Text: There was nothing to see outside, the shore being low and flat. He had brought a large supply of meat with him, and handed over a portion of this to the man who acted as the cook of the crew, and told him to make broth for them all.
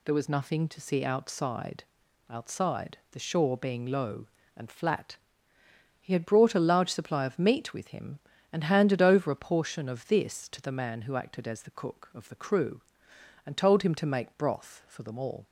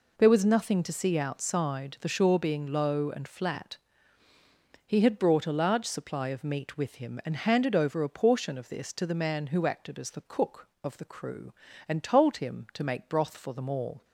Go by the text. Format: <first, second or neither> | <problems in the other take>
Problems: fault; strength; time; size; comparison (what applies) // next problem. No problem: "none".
second | says "outside" twice; at 2.2 s